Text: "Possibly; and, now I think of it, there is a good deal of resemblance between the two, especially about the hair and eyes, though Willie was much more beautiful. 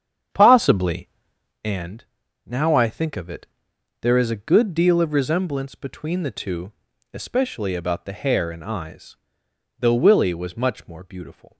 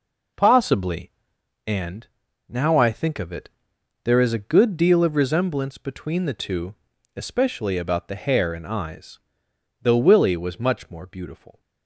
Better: second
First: starts louder than the rest; strong; until 1.6 s; 8 dB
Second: none

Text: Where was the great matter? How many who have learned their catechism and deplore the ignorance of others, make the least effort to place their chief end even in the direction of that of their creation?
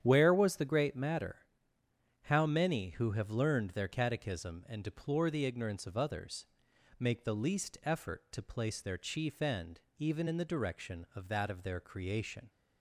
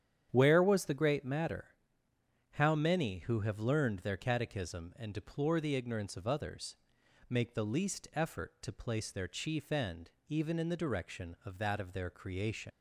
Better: first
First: starts louder than the rest; strong; until 1.0 s; 9 dB // pauses between "end" and "even"; slight; at 9.8 s; 0.16 s long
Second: starts louder than the rest; strong; until 1.3 s; 9 dB // pauses between "end" and "even"; slight; at 10.1 s; 0.16 s long // leaves "creation" unfinished; at 12.7 s; 90 ms

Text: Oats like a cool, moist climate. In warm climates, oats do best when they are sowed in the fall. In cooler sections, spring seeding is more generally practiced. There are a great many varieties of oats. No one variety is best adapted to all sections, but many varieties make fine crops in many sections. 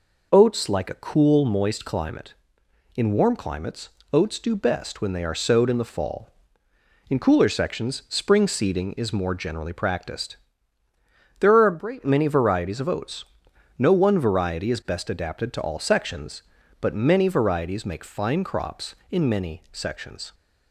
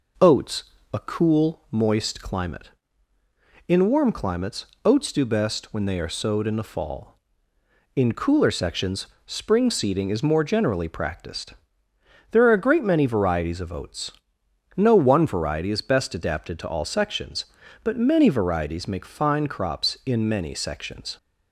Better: first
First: none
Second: skips "like"; at 0.7 s

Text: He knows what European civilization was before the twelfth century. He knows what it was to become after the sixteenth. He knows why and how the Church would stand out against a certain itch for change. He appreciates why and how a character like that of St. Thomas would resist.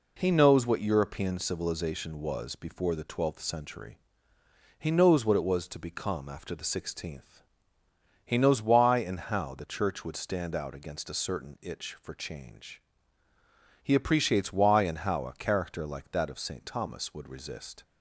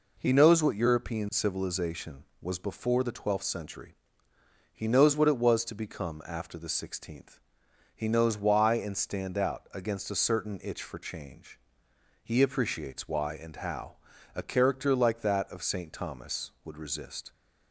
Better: first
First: none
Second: skips "how the Church would"; at 8.9 s // pauses between "how" and "a"; at 13.9 s; 0.38 s long

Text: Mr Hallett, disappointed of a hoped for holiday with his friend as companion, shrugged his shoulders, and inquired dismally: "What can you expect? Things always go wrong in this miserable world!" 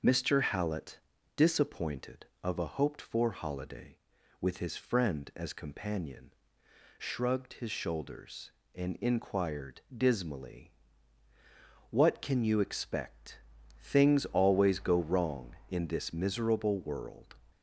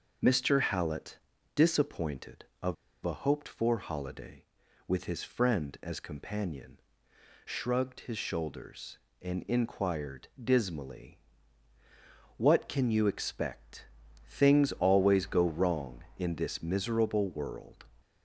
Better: first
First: none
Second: pauses between "of" and "a"; slight; at 2.7 s; 0.29 s long

